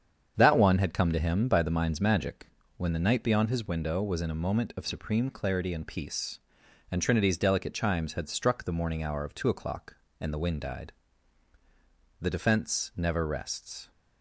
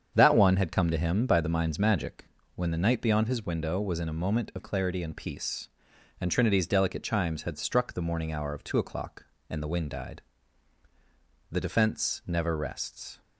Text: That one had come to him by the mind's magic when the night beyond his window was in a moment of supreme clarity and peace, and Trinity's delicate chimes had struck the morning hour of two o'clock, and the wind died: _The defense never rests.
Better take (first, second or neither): first